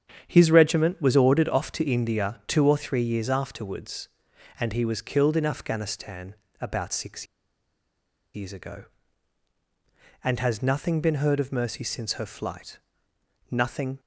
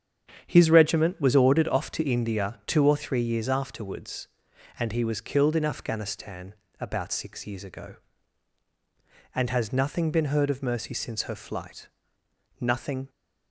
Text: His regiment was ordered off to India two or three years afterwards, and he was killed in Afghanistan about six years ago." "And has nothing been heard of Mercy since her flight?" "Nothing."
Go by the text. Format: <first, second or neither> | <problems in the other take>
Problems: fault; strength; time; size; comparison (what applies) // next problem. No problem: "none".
second | starts louder than the rest; strong; until 1.2 s; 8.5 dB; strong in the second // pauses between "Afghanistan" and "about"; slight; at 6.3 s; 0.28 s long; slight in the second // pauses between "six" and "years"; at 7.2 s; 1.0 s long